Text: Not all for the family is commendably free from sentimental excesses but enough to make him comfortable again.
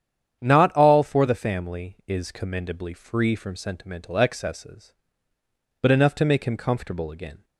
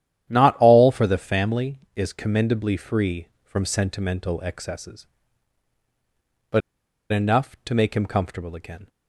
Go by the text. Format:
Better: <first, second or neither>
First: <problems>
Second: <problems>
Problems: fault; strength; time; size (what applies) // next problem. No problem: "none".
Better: first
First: starts louder than the rest; strong; until 1.4 s; 9 dB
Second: starts louder than the rest; strong; until 1.3 s; 11 dB // pauses between "but" and "enough"; noticeable; at 6.6 s; 0.51 s long